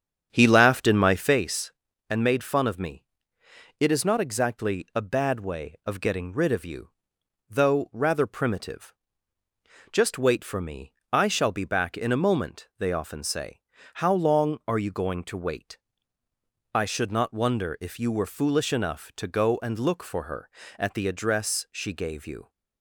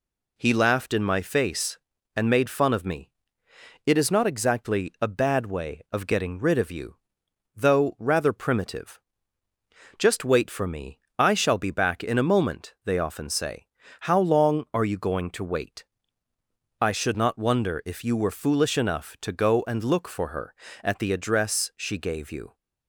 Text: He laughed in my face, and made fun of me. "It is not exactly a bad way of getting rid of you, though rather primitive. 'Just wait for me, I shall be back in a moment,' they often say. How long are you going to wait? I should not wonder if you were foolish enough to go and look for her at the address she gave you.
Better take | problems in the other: second | starts louder than the rest; strong; until 1.5 s; 8 dB

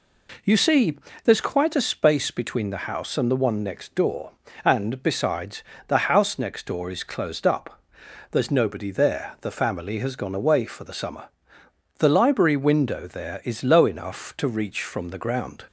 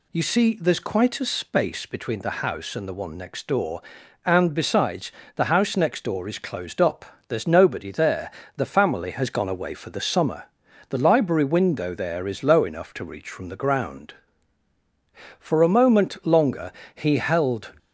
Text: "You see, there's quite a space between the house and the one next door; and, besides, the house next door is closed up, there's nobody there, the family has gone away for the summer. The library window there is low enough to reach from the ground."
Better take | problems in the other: first | goes on to say "For a moment longer he held"; strong; from 15.3 s on; 2.3 s long

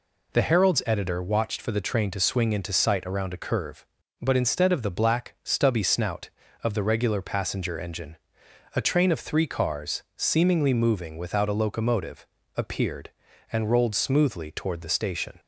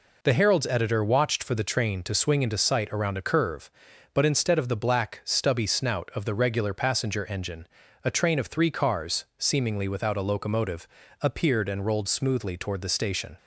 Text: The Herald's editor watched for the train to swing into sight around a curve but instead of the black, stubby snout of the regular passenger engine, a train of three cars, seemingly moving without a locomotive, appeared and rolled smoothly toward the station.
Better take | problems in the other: first | skips "moving"; at 9.8 s

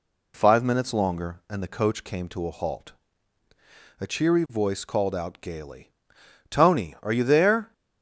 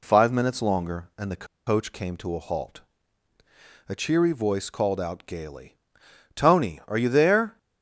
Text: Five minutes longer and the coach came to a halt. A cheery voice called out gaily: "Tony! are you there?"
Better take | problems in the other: first | pauses between "the" and "coach"; slight; at 1.4 s; 0.21 s long

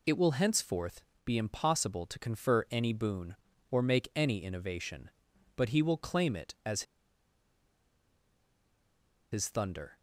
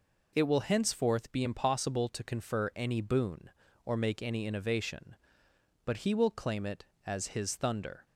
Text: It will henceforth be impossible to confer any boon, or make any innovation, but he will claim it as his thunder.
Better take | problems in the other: second | pauses between "henceforth" and "be"; slight; at 1.0 s; 0.22 s long // pauses between "as" and "his"; strong; at 6.8 s; 2.4 s long

